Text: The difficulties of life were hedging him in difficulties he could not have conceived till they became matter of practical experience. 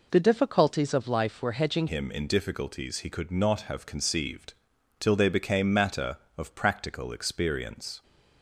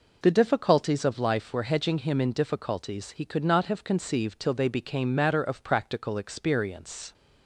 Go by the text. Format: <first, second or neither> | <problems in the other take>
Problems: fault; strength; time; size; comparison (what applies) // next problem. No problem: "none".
second | changes voice at "him"; from 1.8 s on; 6.2 s long // pauses between "conceived" and "till"; at 4.5 s; 0.44 s long